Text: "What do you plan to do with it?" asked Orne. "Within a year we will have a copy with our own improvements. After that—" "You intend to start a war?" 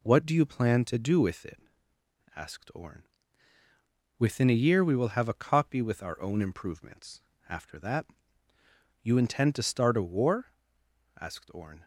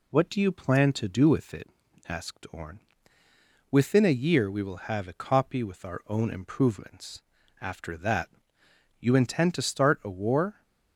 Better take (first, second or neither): second